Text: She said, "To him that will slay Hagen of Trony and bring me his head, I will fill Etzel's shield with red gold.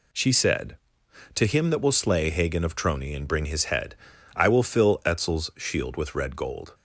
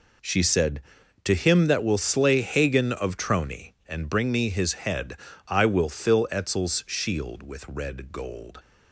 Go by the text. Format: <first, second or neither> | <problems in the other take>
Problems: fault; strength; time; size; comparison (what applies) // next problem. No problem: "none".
second | skips "me"; at 3.4 s